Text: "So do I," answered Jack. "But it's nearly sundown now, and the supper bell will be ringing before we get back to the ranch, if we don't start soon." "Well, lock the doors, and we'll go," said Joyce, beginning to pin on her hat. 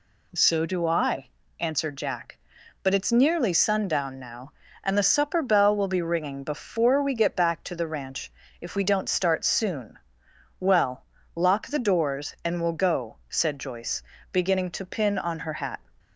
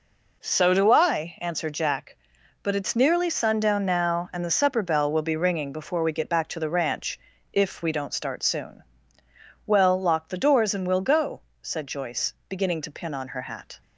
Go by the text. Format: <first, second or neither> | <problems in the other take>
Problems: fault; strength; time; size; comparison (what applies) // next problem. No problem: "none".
neither | none